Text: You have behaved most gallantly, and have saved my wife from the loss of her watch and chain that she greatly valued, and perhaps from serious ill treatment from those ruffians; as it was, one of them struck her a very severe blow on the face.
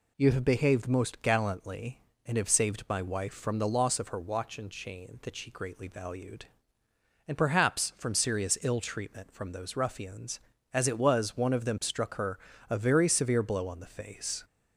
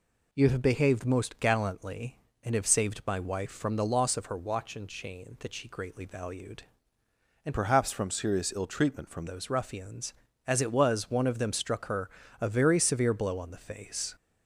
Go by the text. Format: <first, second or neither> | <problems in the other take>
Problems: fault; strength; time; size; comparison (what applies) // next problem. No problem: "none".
first | changes voice from "perhaps" to "from"; from 7.5 to 9.2 s; 1.7 s long // pauses between "her" and "a"; slight; at 12.0 s; 0.32 s long; slight in the first